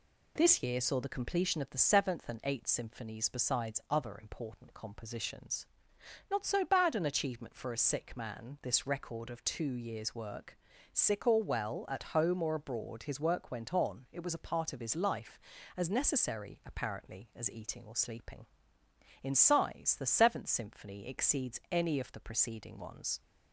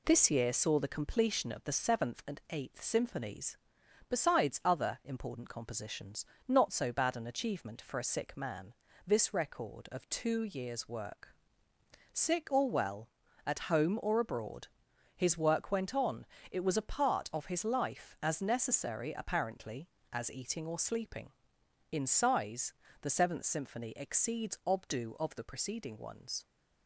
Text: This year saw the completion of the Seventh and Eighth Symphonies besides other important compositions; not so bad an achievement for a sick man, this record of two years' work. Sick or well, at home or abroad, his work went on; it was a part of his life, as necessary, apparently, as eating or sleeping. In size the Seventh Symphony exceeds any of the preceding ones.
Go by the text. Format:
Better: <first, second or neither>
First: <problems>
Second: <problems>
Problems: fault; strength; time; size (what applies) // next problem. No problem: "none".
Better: first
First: none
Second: pauses between "Symphonies" and "besides"; noticeable; at 3.5 s; 0.54 s long // pauses between "size" and "the"; slight; at 22.7 s; 0.26 s long // says "obdu" for "any"; at 24.6 s